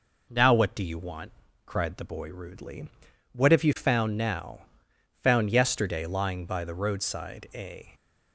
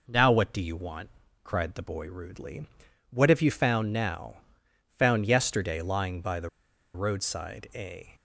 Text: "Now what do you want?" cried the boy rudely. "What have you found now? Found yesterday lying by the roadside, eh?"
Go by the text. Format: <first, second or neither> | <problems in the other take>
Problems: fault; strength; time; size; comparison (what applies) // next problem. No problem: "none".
first | pauses between "the" and "roadside"; at 6.4 s; 0.45 s long